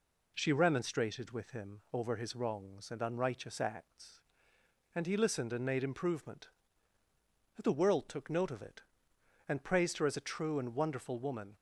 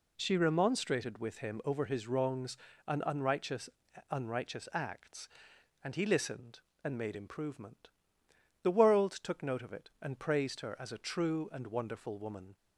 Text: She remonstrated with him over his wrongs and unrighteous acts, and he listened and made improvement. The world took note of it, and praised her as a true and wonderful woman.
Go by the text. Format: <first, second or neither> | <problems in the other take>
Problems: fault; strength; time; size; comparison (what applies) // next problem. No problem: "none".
first | says "unrighteous" twice; at 4.1 s